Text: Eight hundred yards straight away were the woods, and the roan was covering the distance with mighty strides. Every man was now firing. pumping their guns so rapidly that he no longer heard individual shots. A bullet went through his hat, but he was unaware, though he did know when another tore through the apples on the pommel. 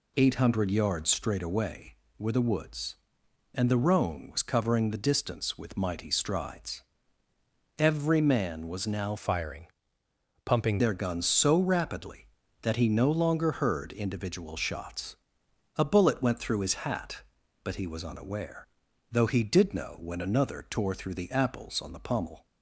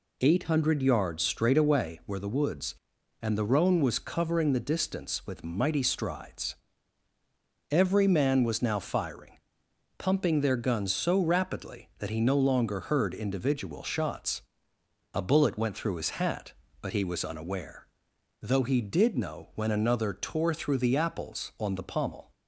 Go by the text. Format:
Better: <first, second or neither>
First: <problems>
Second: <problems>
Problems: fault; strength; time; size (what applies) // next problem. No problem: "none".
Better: second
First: changes voice from "firing" to "pumping"; from 9.1 to 10.7 s; 1.6 s long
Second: none